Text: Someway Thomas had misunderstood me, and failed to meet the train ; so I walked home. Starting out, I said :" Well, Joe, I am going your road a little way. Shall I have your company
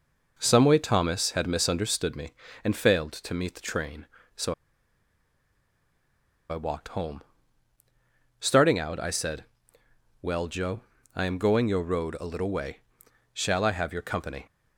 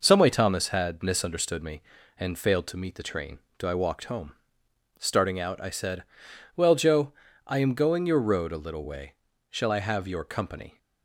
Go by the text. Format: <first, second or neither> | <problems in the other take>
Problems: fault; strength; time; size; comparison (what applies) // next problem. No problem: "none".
second | pauses between "so" and "I"; strong; at 4.5 s; 1.9 s long